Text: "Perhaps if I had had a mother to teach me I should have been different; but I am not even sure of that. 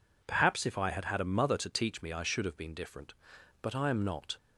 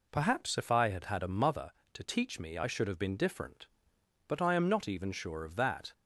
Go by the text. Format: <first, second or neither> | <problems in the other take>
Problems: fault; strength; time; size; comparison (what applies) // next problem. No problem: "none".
second | stops before "even sure of that"; at 4.3 s